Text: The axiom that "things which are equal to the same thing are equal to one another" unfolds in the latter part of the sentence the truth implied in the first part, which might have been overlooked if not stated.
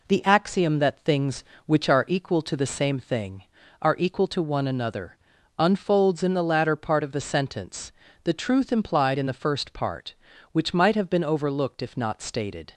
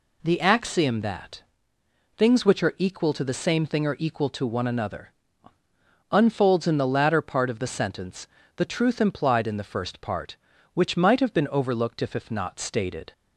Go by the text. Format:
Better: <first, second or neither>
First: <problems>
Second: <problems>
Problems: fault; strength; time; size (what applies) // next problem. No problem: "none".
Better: first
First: pauses between "another" and "unfolds"; at 5.1 s; 0.40 s long // pauses between "sentence" and "the"; slight; at 7.9 s; 0.32 s long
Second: pauses between "that" and "things"; noticeable; at 1.4 s; 0.76 s long // pauses between "another" and "unfolds"; noticeable; at 5.1 s; 0.98 s long // pauses between "sentence" and "the"; slight; at 8.2 s; 0.30 s long // says "if" twice; at 12.1 s